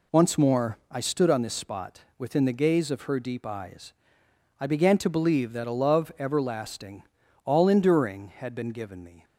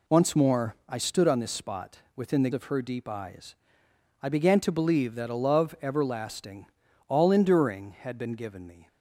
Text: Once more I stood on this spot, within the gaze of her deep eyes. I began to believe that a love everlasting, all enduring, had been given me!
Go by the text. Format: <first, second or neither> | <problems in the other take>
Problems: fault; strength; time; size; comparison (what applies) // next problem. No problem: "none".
first | skips "gaze"; at 2.5 s